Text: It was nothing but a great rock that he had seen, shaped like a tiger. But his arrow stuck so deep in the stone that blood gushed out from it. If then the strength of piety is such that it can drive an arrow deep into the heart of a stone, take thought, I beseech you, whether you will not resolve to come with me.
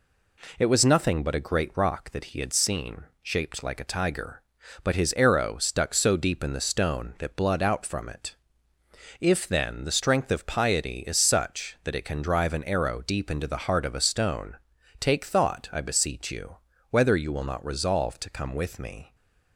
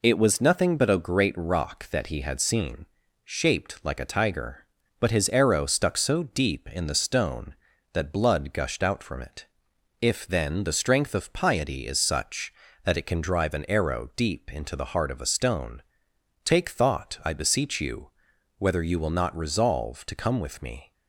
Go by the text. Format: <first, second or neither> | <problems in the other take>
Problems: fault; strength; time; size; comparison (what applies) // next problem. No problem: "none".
second | skips "gushed"; at 7.6 s